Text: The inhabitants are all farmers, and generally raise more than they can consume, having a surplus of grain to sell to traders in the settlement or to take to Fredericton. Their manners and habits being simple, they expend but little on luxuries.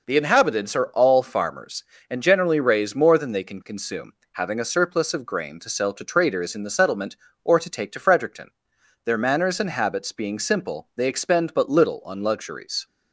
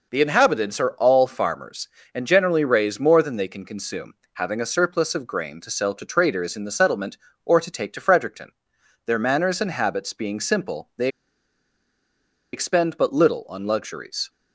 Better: first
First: none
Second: pauses between "they" and "expend"; strong; at 11.0 s; 1.4 s long

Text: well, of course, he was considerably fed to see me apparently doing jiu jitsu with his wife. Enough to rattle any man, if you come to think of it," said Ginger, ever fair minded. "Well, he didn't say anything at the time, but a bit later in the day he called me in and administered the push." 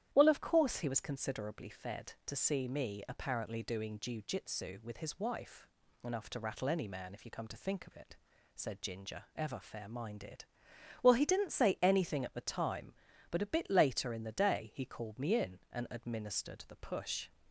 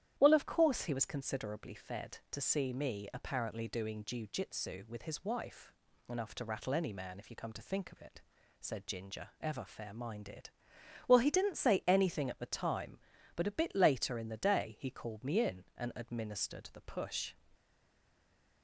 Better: first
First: starts louder than the rest; strong; until 1.1 s; 11 dB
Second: starts louder than the rest; strong; until 1.1 s; 11 dB // stays silent after the last word; from 17.5 s on; 1.1 s long

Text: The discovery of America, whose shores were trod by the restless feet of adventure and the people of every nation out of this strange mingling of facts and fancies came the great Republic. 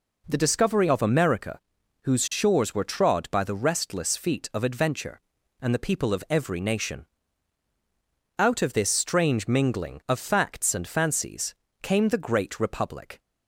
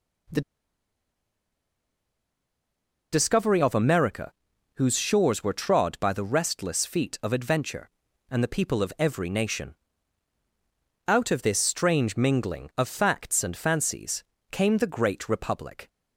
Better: first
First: pauses between "nation" and "out"; strong; at 7.0 s; 1.3 s long // pauses between "fancies" and "came"; slight; at 11.5 s; 0.28 s long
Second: pauses between "The" and "discovery"; strong; at 0.4 s; 2.6 s long // pauses between "nation" and "out"; strong; at 9.7 s; 1.3 s long // pauses between "fancies" and "came"; slight; at 14.2 s; 0.28 s long

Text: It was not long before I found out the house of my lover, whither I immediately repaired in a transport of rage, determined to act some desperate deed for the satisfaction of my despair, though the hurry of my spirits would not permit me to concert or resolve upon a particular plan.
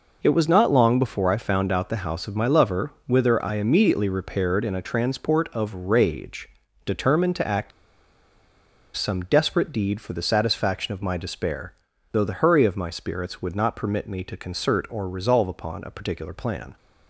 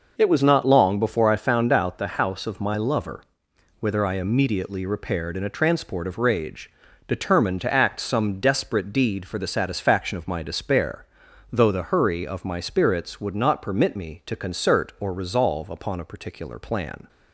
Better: second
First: pauses between "act" and "some"; strong; at 7.7 s; 1.2 s long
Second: none

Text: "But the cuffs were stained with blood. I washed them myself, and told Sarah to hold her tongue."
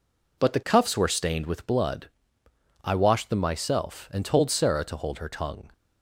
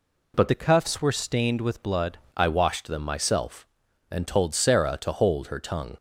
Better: first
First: none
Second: changes voice from "the" to "blood"; from 0.4 to 2.1 s; 1.7 s long

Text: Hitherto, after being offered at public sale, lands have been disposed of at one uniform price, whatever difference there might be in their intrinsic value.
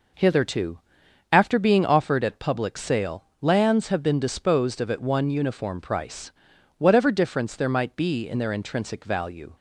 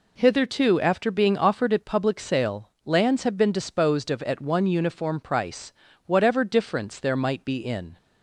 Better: first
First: none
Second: stops before "their intrinsic value"; at 7.9 s

